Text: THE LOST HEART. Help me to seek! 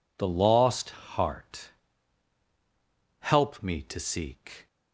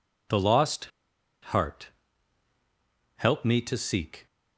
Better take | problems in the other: first | pauses between "LOST" and "HEART"; noticeable; at 0.8 s; 0.65 s long

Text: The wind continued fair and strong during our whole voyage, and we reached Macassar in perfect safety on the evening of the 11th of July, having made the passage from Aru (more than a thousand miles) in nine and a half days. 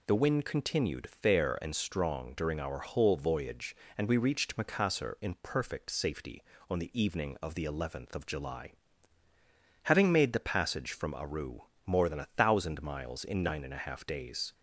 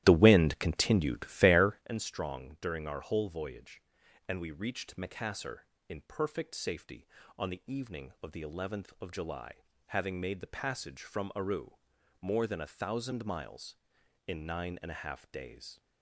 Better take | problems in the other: first | starts louder than the rest; strong; until 1.9 s; 14 dB

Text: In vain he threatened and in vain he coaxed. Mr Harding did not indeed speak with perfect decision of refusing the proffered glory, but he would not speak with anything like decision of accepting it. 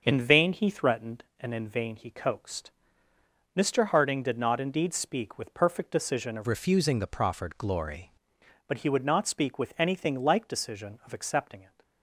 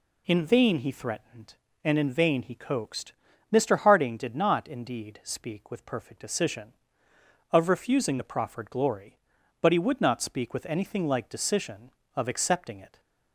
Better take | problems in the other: second | starts louder than the rest; until 1.0 s; 6.5 dB // changes voice from "refusing" to "glory"; from 6.4 to 8.1 s; 1.7 s long

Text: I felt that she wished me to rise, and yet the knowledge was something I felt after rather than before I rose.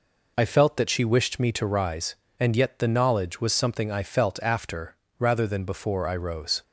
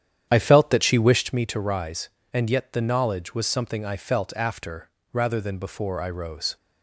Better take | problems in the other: first | starts louder than the rest; strong; until 1.4 s; 9.5 dB // pauses between "after" and "rather"; slight; at 4.8 s; 0.22 s long; slight in the first

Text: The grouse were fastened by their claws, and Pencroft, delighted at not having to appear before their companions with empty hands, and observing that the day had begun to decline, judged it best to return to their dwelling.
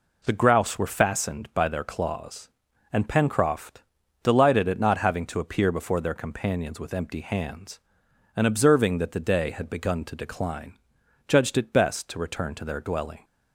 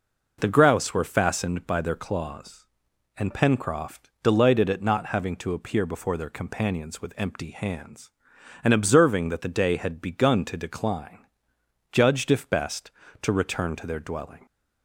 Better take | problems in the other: first | says "if" for "it"; at 12.3 s

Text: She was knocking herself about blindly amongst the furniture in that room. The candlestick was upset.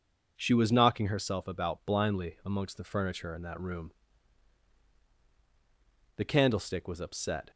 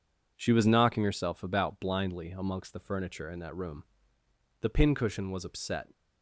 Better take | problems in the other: first | says "pincushion" for "candlestick"; at 4.6 s

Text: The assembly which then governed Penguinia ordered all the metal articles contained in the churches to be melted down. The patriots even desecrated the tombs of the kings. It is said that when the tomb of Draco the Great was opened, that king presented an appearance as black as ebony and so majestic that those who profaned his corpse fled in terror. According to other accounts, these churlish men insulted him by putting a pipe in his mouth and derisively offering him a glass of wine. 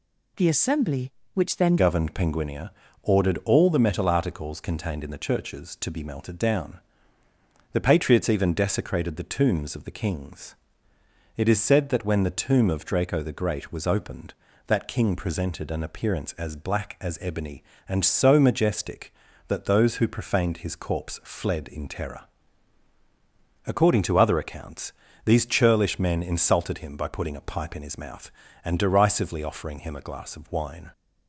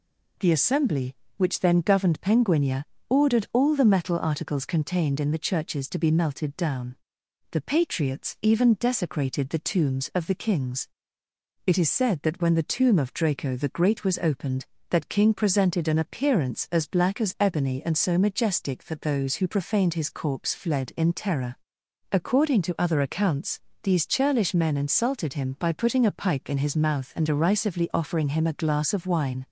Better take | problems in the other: second | changes voice at "governed"; from 1.7 s on; 29.2 s long // pauses between "Penguinia" and "ordered"; slight; at 2.6 s; 0.32 s long; slight in the second

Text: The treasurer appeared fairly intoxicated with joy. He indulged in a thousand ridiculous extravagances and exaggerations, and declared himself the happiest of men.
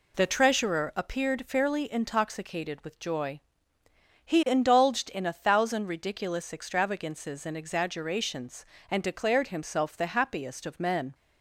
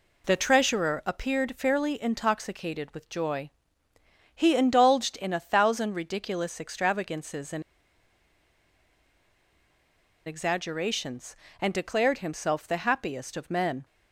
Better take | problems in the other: first | pauses between "and" and "exaggerations"; strong; at 7.6 s; 2.6 s long

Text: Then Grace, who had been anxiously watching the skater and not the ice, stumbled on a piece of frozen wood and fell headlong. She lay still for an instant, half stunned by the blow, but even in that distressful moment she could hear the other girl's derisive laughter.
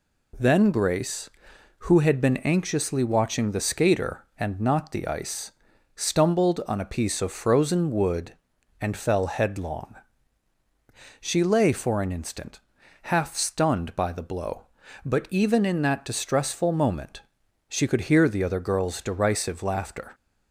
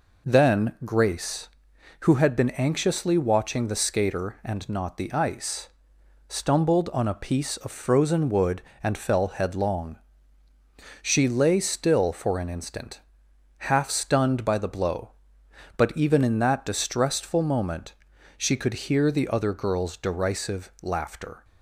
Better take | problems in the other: second | skips "still"; at 11.7 s // pauses between "moment" and "she"; noticeable; at 17.2 s; 0.48 s long; noticeable in the second

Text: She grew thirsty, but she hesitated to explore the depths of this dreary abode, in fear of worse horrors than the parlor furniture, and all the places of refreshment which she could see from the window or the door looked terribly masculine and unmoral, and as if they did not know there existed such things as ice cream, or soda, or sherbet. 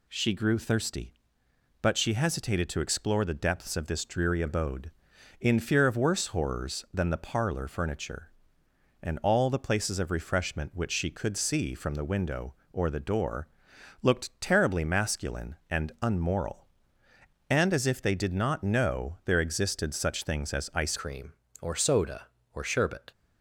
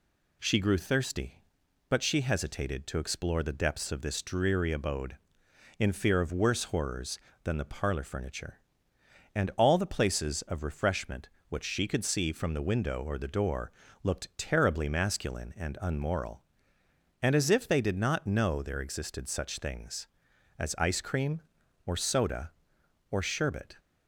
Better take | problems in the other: second | pauses between "door" and "looked"; noticeable; at 13.4 s; 0.54 s long; slight in the second // changes voice at "cream"; from 20.9 s on; 2.2 s long

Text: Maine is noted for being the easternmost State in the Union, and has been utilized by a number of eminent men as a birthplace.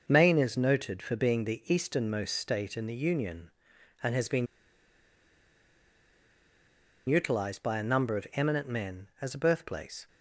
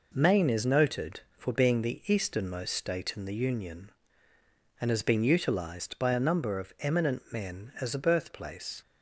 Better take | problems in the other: second | pauses between "been" and "utilized"; strong; at 4.4 s; 2.6 s long

